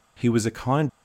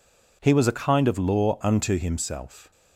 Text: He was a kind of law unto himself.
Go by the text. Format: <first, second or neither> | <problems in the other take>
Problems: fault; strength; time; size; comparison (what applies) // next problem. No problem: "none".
second | stops before "of law unto himself"; at 0.8 s